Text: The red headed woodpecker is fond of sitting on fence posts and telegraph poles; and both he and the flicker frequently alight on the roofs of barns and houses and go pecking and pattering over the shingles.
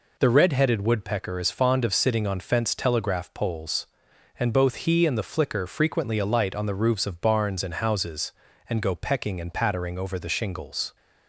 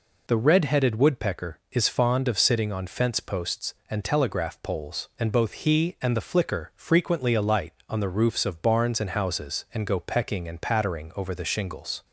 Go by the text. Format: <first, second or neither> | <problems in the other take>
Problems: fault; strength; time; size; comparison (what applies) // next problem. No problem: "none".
second | skips "posts and"; at 2.7 s